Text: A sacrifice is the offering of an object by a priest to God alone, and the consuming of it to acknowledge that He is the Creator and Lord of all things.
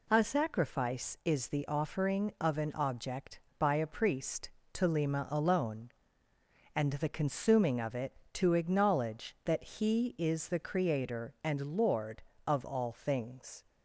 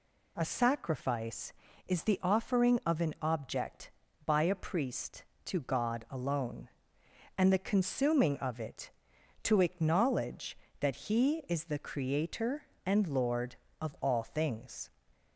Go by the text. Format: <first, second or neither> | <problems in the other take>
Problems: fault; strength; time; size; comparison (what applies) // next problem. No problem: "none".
second | says "Lima" for "God"; at 4.8 s